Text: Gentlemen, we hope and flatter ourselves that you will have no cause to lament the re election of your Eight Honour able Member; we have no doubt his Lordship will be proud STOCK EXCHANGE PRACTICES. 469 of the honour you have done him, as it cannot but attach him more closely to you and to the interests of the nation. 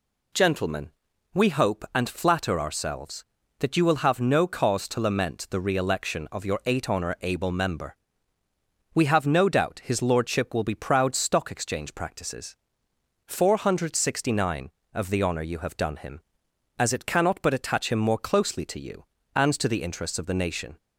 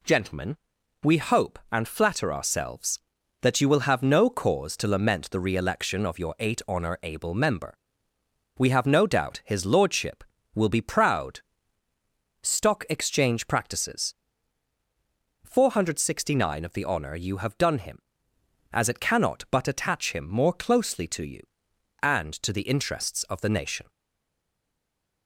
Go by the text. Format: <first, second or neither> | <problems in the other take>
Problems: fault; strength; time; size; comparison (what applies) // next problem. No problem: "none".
first | pauses between "proud" and "STOCK"; at 11.4 s; 1.0 s long // stays silent after the last word; noticeable; from 23.8 s on; 1.4 s long